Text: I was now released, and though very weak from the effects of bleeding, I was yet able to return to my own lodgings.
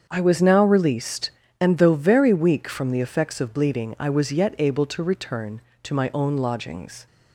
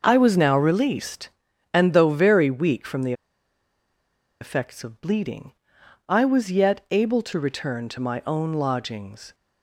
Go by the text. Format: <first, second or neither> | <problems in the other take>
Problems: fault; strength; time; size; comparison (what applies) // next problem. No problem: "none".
first | starts louder than the rest; noticeable; until 1.0 s; 6 dB; also in the first // pauses between "the" and "effects"; strong; at 3.1 s; 1.2 s long